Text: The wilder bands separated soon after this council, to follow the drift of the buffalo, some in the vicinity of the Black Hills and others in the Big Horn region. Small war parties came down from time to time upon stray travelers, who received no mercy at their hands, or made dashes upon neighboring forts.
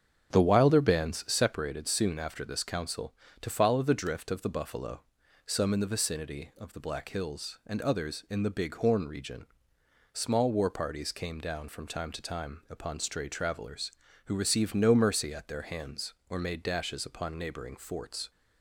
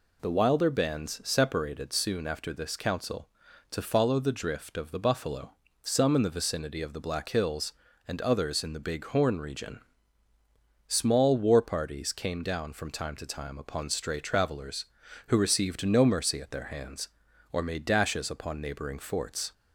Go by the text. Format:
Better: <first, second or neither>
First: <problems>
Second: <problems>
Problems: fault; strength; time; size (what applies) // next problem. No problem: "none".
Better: second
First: starts louder than the rest; strong; until 1.5 s; 8 dB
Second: none